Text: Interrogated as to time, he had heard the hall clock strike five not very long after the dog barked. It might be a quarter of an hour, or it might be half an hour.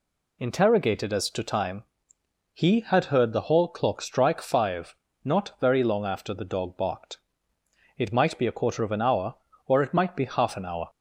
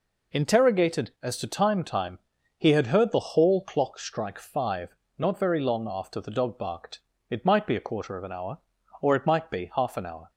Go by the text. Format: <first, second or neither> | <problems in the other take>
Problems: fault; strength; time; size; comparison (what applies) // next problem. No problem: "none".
first | says "time" twice; at 1.8 s // pauses between "five" and "not"; slight; at 4.9 s; 0.24 s long; slight in the first